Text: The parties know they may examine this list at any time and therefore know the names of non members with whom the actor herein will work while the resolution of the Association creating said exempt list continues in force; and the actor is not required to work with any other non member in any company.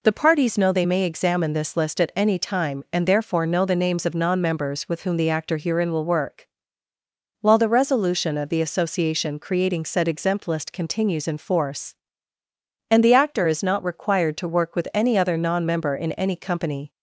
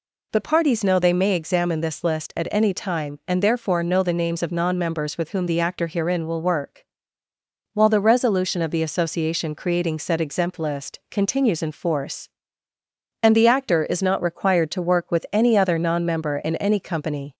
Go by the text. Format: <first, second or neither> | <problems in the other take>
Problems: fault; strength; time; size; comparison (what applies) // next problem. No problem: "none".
neither | pauses between "work" and "while"; noticeable; the same in both